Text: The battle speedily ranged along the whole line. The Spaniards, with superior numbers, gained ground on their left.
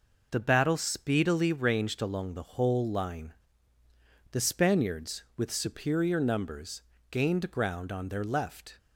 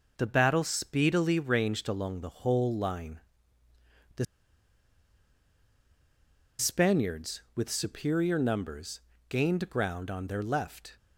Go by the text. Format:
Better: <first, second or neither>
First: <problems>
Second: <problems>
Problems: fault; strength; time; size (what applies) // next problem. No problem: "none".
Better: first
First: none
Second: pauses between "The" and "Spaniards"; strong; at 4.2 s; 2.3 s long